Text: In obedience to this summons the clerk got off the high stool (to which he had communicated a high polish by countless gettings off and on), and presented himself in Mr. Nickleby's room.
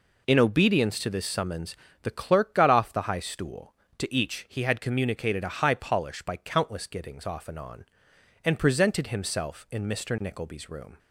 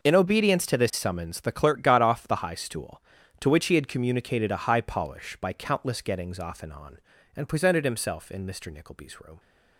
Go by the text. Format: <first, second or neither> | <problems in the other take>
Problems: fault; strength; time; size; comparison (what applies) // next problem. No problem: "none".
second | pauses between "summons" and "the"; slight; at 1.7 s; 0.26 s long // says "each" for "which"; at 4.1 s